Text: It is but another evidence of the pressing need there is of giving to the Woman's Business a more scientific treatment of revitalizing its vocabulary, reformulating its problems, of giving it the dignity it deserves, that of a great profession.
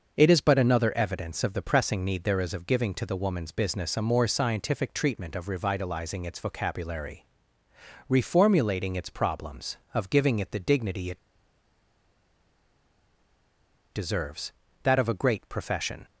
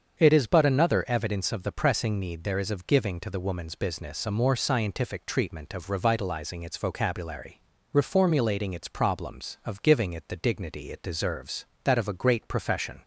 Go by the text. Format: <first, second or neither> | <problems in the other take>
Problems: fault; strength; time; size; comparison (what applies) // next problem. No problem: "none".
second | starts louder than the rest; noticeable; until 1.1 s; 6 dB; also in the second // pauses between "it" and "deserves"; strong; at 11.1 s; 2.7 s long